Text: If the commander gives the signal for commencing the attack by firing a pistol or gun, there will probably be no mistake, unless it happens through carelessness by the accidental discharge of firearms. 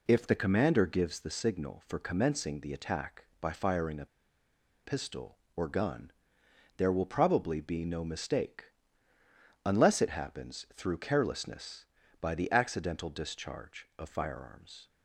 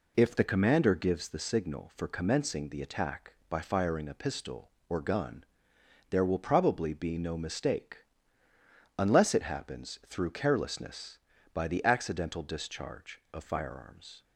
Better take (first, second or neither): second